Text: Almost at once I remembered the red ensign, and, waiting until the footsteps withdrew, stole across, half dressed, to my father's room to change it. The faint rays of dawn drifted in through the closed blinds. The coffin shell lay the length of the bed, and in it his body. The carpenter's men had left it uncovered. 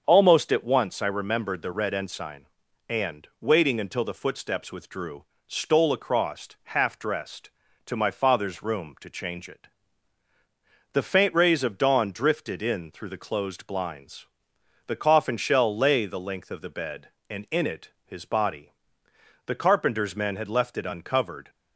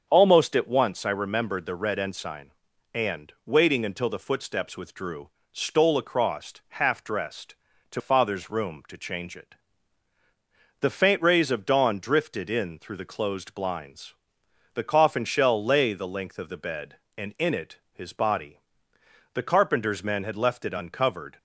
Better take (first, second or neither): first